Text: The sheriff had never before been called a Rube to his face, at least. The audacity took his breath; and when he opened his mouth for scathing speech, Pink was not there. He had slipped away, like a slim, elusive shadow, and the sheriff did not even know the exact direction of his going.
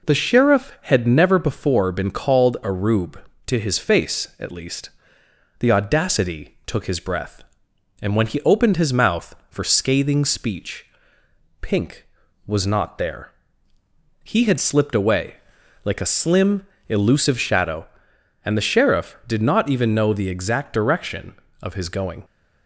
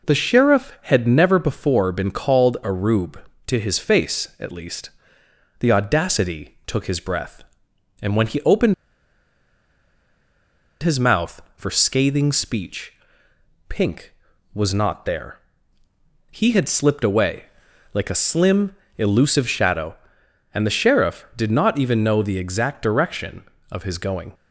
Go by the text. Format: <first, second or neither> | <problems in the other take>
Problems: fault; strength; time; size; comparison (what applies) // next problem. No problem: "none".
first | pauses between "opened" and "his"; strong; at 8.7 s; 2.0 s long